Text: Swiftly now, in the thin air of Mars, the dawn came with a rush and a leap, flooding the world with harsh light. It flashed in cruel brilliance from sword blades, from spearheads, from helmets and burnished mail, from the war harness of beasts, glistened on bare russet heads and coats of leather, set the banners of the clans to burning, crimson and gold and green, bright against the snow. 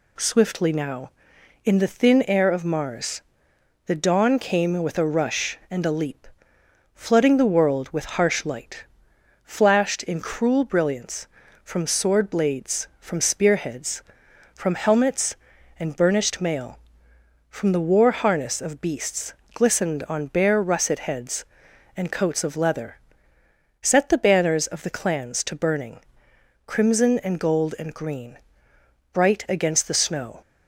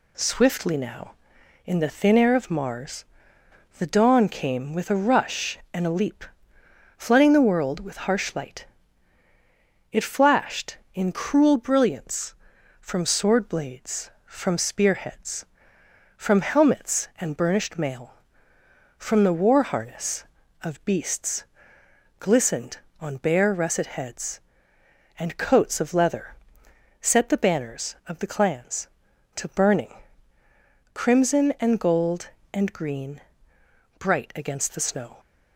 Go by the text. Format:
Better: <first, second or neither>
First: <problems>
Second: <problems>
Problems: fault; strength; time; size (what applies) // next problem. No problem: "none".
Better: second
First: skips "It"; at 9.1 s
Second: none